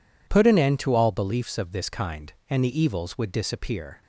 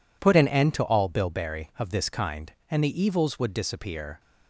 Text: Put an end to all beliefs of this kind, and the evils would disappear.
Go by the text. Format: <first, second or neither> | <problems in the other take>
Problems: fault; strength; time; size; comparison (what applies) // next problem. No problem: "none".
first | says "bilberry" for "beliefs"; at 1.0 s